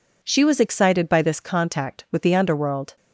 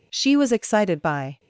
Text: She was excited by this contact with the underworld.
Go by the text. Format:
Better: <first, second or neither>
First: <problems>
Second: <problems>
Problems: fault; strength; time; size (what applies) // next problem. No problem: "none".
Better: first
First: none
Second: stops before "this contact with the underworld"; at 1.3 s